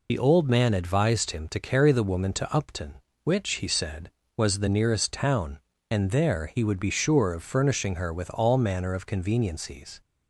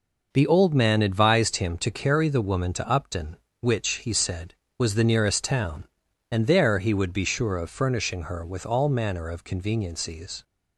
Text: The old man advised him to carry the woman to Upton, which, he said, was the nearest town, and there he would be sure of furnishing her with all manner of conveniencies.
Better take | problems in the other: second | loses the start of "The"; at 0.0 s; 35 ms

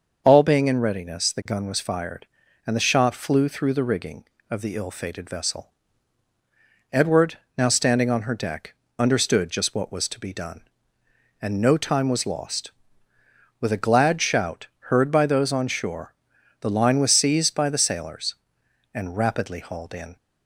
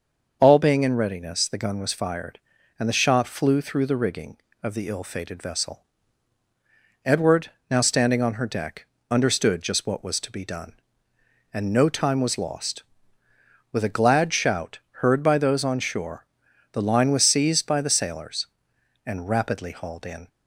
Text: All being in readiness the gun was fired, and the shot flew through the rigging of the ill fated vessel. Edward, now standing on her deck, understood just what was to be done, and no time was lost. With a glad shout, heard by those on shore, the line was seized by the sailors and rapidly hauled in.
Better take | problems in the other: neither | starts louder than the rest; the same in both

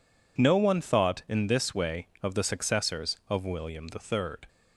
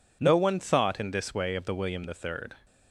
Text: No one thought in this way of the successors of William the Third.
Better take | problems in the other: first | skips "successors of"; at 1.7 s

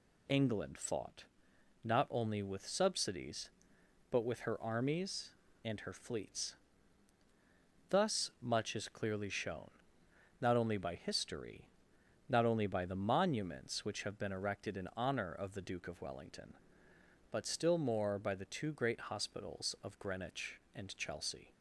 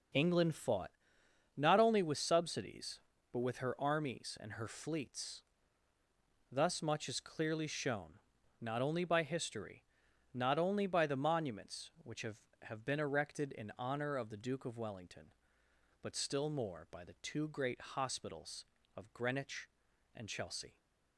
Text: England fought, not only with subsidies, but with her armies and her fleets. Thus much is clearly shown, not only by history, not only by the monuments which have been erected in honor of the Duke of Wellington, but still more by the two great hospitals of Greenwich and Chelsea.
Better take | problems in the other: first | says "have" twice; at 12.6 s

